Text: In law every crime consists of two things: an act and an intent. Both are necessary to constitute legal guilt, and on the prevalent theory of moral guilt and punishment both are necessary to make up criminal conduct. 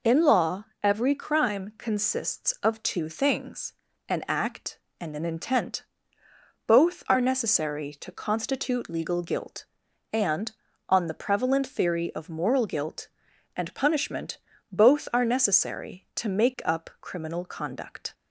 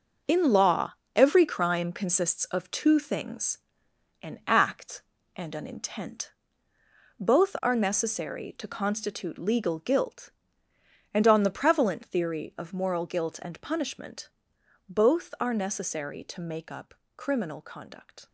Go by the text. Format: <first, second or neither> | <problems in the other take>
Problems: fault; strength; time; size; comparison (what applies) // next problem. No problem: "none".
first | gets quieter; strong; throughout; 9 dB // pauses between "law" and "every"; slight; at 0.9 s; 0.20 s long; slight in the first // pauses between "punishment" and "both"; noticeable; at 14.2 s; 0.60 s long; slight in the first // pauses between "up" and "criminal"; slight; at 16.9 s; 0.22 s long